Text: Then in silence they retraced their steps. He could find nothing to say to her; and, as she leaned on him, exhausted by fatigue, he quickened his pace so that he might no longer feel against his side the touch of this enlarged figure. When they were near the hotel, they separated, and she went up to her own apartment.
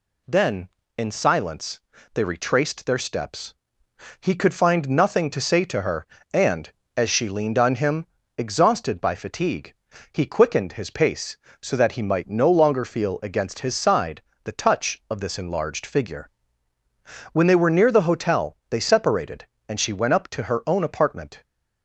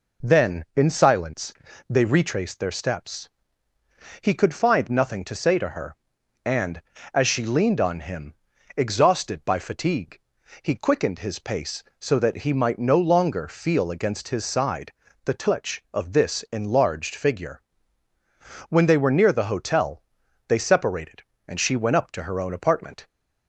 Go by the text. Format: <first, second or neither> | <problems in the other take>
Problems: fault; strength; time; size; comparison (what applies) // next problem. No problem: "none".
neither | pauses between "silence" and "they"; the same in both // pauses between "side" and "the"; slight; the same in both